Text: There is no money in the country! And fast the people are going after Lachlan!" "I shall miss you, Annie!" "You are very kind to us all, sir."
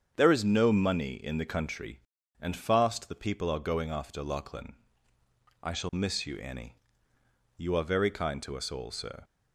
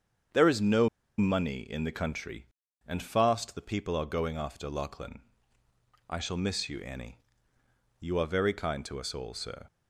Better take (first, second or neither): first